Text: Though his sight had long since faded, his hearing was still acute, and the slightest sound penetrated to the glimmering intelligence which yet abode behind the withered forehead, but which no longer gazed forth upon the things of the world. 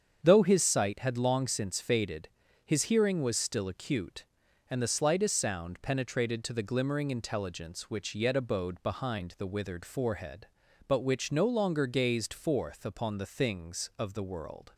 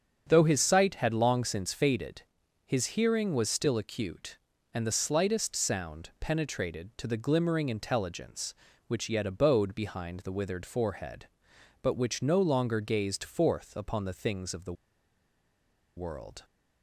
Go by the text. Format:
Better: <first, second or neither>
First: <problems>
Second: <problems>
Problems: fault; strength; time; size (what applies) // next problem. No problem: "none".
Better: first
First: starts louder than the rest; strong; until 1.2 s; 7.5 dB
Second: starts louder than the rest; until 1.2 s; 7 dB // pauses between "the" and "world"; at 14.7 s; 1.2 s long